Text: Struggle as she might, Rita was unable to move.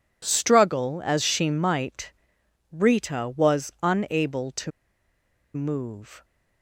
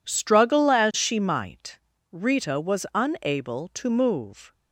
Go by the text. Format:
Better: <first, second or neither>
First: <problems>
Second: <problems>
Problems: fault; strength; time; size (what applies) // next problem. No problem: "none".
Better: second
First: pauses between "to" and "move"; noticeable; at 4.7 s; 0.84 s long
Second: none